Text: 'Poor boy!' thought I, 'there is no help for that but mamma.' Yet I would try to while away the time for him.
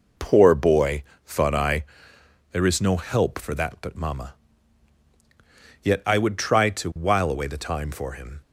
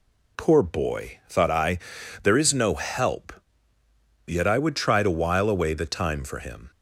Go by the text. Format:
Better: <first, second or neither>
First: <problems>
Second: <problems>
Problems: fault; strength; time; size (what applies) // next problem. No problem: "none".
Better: first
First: none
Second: skips "for that but mamma"; at 3.7 s